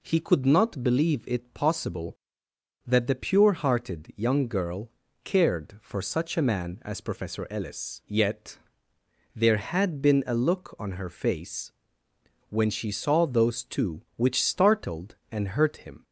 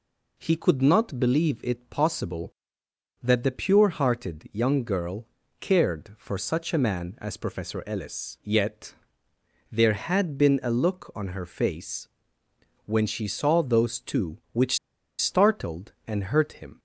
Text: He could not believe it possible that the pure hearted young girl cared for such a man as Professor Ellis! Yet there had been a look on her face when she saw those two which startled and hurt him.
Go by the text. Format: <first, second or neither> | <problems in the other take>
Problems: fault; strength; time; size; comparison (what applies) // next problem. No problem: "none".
first | pauses between "girl" and "cared"; slight; at 5.2 s; 0.34 s long; slight in the first // pauses between "Yet" and "there"; noticeable; at 8.9 s; 0.78 s long; noticeable in the first // pauses between "face" and "when"; noticeable; at 12.0 s; 0.80 s long; noticeable in the first // pauses between "which" and "startled"; at 14.7 s; 0.40 s long